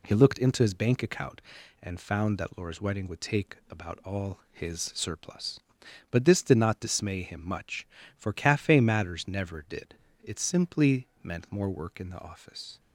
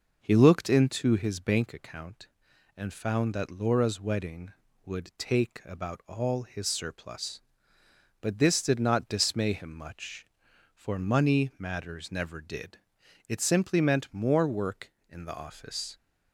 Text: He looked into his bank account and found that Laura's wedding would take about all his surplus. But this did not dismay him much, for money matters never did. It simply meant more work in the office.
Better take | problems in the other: second | says "cafe" for "money"; at 8.3 s

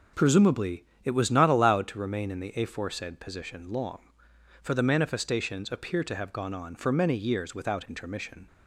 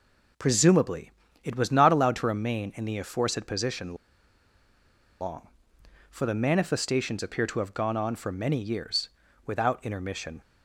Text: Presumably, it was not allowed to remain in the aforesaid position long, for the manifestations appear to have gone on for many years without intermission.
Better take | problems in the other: first | pauses between "position" and "long"; strong; at 3.9 s; 1.2 s long // pauses between "years" and "without"; slight; at 9.0 s; 0.36 s long

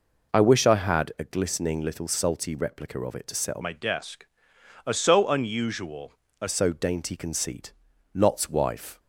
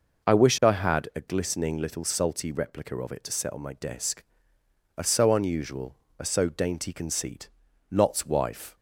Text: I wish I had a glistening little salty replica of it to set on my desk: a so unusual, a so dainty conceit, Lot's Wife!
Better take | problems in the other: second | changes voice from "my" to "a"; from 3.6 to 6.4 s; 2.8 s long

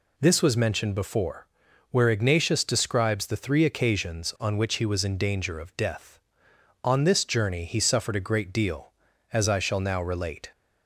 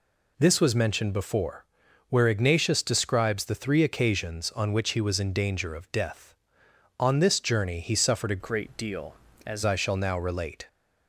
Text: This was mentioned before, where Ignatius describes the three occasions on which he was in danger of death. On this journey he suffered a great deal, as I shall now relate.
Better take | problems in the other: first | changes voice from "great" to "as"; from 8.4 to 9.6 s; 1.2 s long

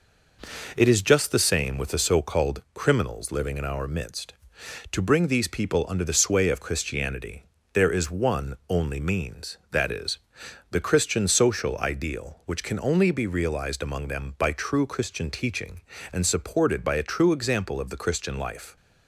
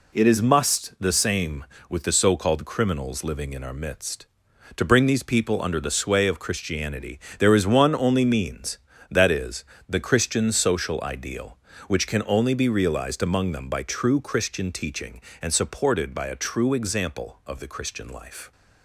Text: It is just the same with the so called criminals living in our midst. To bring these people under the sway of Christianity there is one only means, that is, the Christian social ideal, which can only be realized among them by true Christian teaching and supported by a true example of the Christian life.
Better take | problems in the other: first | says "must" for "just"; at 0.4 s // pauses between "Christianity" and "there"; slight; at 7.1 s; 0.20 s long; slight in the first

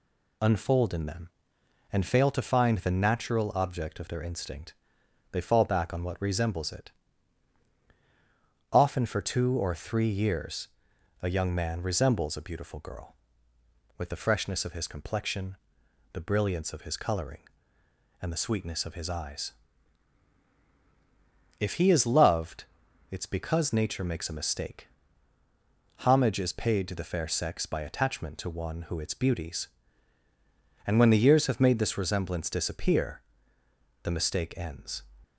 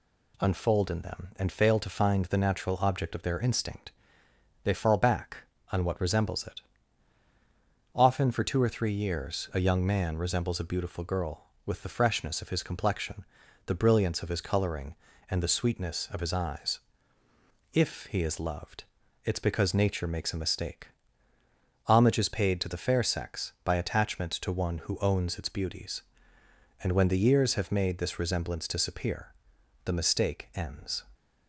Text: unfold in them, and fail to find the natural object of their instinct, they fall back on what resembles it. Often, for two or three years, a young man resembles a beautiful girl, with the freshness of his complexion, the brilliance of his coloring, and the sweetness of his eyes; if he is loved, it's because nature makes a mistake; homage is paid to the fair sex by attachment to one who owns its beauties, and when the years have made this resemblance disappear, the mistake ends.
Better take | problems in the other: second | skips "owns"; at 28.9 s

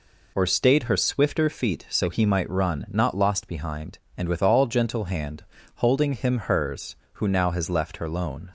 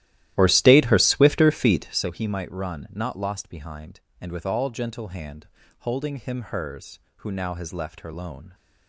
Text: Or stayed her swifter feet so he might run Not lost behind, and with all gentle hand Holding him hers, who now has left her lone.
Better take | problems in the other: first | starts louder than the rest; strong; until 2.1 s; 14 dB // pauses between "hand" and "Holding"; slight; at 5.4 s; 0.32 s long; slight in the first

